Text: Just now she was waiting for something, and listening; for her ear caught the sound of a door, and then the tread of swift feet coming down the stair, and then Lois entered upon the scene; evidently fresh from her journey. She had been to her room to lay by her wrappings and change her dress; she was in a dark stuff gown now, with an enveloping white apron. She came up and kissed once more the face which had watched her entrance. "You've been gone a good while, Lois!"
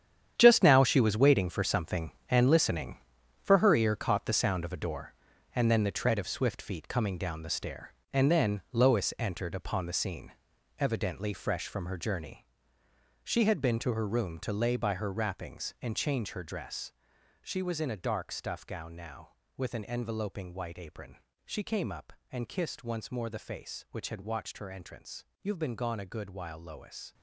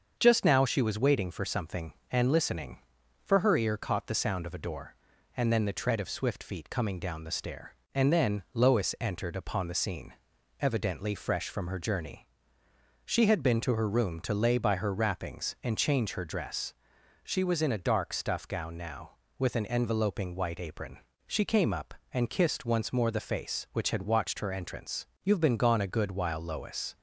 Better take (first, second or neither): second